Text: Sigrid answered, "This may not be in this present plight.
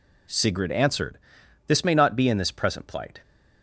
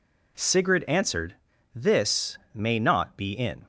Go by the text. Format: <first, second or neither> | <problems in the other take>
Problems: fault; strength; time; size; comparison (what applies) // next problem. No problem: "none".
first | pauses between "This" and "may"; slight; at 2.3 s; 0.16 s long // stops before "this present plight"; at 3.6 s